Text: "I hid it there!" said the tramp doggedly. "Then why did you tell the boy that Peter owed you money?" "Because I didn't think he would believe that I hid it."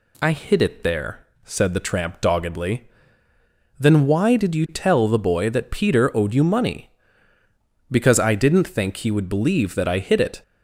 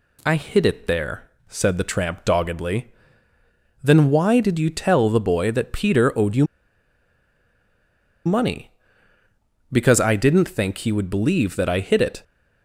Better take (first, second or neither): first